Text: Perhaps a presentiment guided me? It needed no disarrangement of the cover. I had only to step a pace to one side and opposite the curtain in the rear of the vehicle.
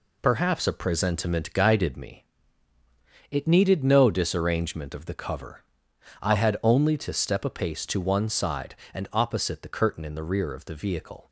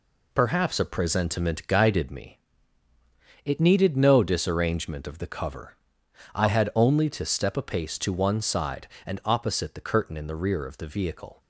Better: neither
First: none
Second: none

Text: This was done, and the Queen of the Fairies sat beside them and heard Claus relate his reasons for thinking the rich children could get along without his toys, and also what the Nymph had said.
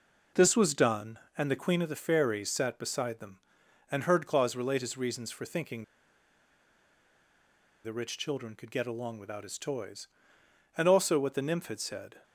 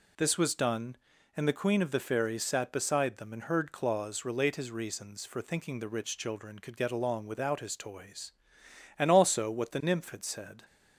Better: second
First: pauses between "thinking" and "the"; strong; at 5.8 s; 2.0 s long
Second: none

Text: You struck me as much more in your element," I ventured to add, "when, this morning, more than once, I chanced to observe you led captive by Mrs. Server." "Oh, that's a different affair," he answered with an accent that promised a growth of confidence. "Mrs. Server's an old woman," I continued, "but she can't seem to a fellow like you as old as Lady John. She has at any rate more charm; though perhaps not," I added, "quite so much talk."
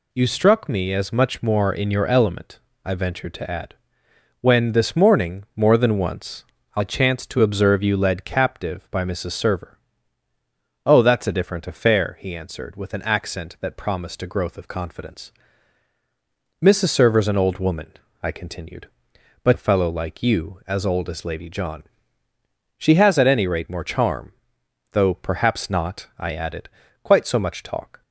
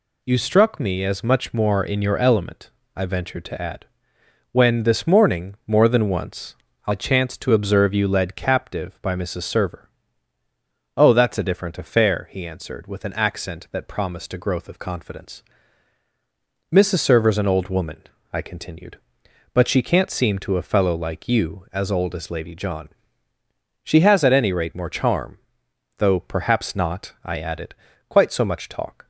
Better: second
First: skips "she can't seem to"; at 19.5 s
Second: none

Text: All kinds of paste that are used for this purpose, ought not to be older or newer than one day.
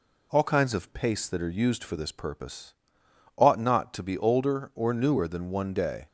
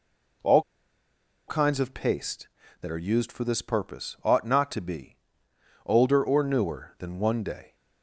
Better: first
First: none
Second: pauses between "All" and "kinds"; noticeable; at 0.6 s; 0.86 s long // pauses between "be" and "older"; noticeable; at 5.1 s; 0.70 s long

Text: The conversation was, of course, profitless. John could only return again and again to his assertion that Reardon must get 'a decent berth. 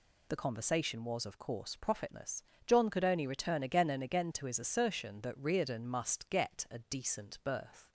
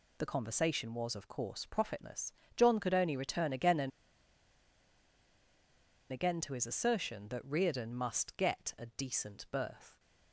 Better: first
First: none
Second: pauses between "and" and "again"; strong; at 3.9 s; 2.2 s long

